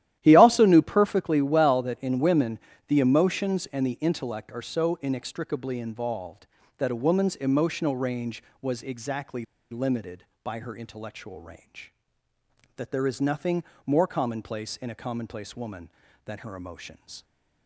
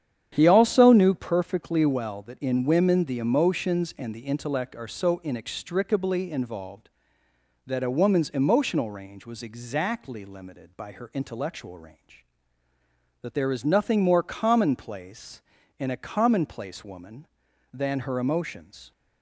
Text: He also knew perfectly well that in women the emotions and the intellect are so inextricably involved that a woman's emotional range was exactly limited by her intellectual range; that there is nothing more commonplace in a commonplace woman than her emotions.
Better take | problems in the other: second | starts louder than the rest; strong; until 1.2 s; 12.5 dB; strong in the second // pauses between "women" and "the"; slight; at 2.5 s; 0.30 s long // pauses between "exactly" and "limited"; slight; at 9.4 s; 0.26 s long // pauses between "nothing" and "more"; slight; at 13.6 s; 0.22 s long

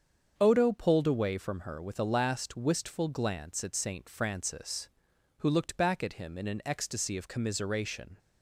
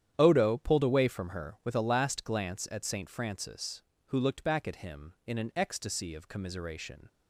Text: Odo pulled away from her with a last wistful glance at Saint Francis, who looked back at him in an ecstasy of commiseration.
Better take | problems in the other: first | starts louder than the rest; strong; until 1.1 s; 10 dB; strong in the first // skips "wistful"; at 2.2 s

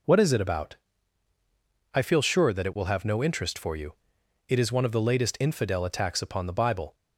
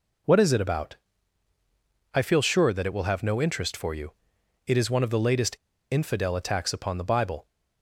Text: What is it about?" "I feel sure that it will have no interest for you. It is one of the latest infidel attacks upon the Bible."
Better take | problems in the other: first | pauses between "latest" and "infidel"; at 5.5 s; 0.37 s long

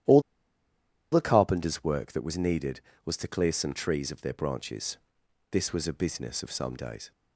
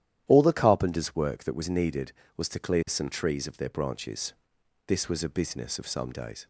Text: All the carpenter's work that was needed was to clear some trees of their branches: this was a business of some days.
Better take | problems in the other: second | starts louder than the rest; strong; until 1.9 s; 11.5 dB; strong in the second // pauses between "All" and "the"; noticeable; at 0.2 s; 0.90 s long

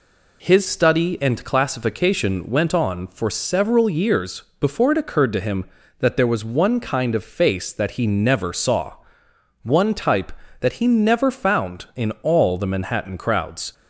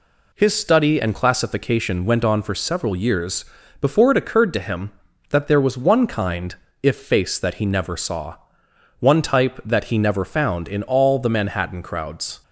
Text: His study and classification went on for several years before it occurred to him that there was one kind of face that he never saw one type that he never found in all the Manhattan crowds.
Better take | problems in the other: first | pauses between "years" and "before"; slight; at 3.4 s; 0.36 s long; slight in the first // says "if" for "of"; at 6.8 s // pauses between "saw" and "one"; noticeable; at 8.3 s; 0.62 s long; noticeable in the first

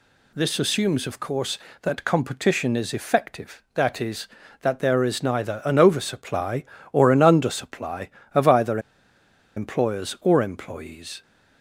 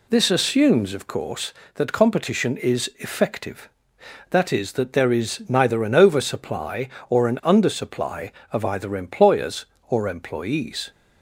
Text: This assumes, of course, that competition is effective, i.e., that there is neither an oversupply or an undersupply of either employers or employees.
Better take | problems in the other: second | pauses between "either" and "employers"; noticeable; at 8.7 s; 0.77 s long

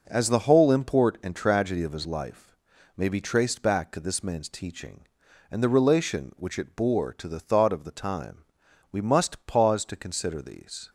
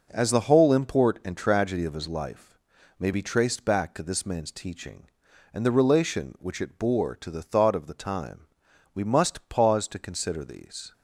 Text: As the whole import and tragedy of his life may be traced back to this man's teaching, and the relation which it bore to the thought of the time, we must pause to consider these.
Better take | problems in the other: neither | starts louder than the rest; noticeable; the same in both // pauses between "life" and "may"; the same in both

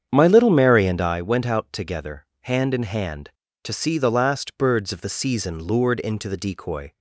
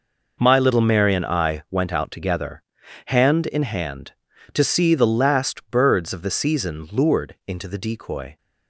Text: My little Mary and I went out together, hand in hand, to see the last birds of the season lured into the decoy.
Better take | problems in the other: second | starts louder than the rest; strong; until 1.2 s; 8 dB

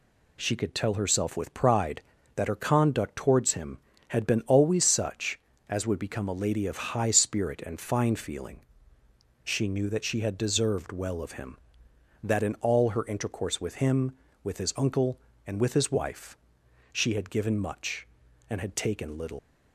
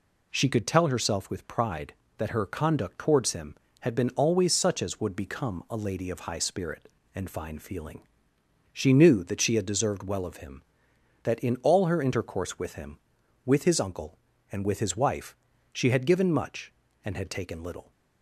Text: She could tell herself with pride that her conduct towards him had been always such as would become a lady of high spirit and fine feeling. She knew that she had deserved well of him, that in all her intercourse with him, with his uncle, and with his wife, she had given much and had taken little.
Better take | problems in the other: second | leaves "little" unfinished; at 19.3 s; 120 ms

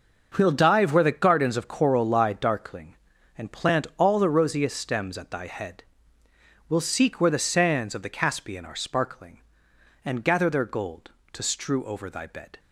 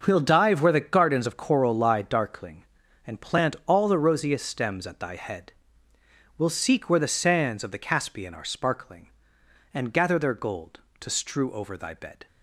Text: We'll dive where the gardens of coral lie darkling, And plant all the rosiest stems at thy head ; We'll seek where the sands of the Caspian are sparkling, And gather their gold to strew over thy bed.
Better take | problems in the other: neither | starts louder than the rest; noticeable; the same in both

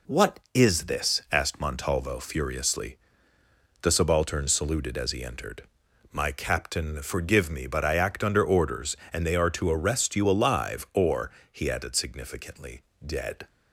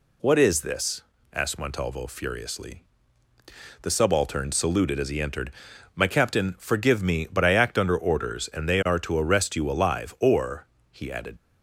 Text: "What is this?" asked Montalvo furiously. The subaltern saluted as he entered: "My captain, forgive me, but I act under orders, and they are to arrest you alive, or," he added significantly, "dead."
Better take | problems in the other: first | stops before "significantly dead"; at 11.3 s

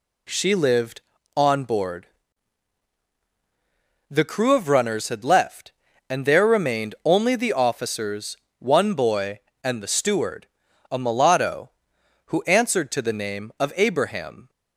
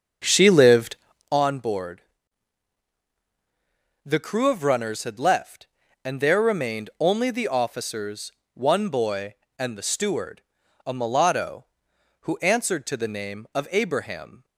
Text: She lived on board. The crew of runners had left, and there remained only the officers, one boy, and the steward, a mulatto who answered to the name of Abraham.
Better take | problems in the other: first | starts louder than the rest; until 1.4 s; 6.5 dB

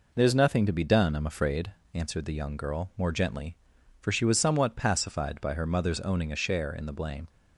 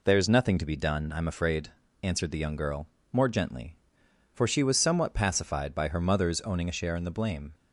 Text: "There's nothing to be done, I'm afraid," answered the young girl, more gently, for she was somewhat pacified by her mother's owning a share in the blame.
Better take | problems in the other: neither | none

